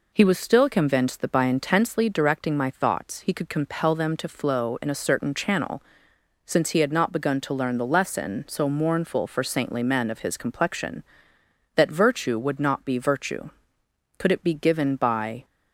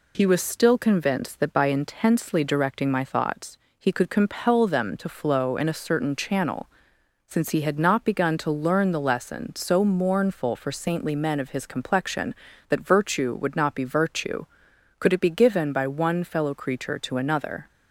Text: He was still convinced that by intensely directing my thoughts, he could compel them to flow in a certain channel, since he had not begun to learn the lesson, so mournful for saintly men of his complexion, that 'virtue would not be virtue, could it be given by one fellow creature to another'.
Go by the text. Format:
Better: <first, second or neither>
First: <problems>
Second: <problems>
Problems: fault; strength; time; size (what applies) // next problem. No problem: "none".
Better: second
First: stops before "one fellow creature to another"; at 15.4 s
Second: none